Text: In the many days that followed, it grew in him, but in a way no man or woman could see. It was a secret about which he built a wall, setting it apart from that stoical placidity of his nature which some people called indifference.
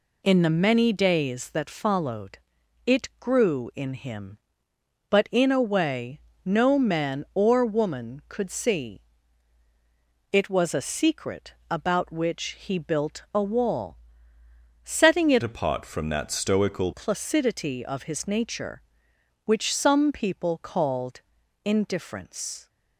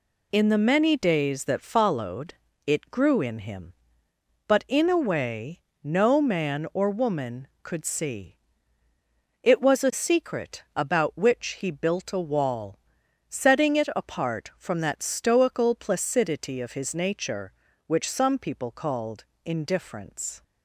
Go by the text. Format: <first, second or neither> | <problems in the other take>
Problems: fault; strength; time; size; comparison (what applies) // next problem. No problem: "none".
second | pauses between "way" and "no"; slight; at 6.1 s; 0.26 s long; slight in the second // pauses between "secret" and "about"; slight; at 11.5 s; 0.16 s long // changes voice from "apart" to "stoical"; from 15.4 to 16.9 s; 1.5 s long // pauses between "called" and "indifference"; at 21.1 s; 0.44 s long; slight in the second